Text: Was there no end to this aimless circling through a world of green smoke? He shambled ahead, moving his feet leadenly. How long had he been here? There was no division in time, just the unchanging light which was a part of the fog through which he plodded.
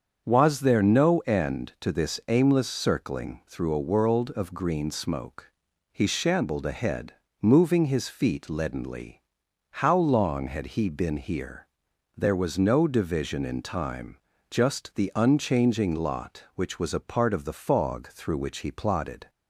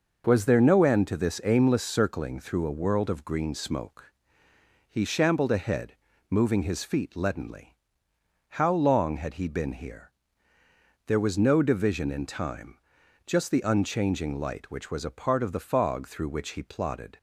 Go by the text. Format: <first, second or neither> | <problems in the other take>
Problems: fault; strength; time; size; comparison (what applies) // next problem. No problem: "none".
second | starts louder than the rest; until 1.2 s; 7 dB // says "lot" for "light"; at 15.9 s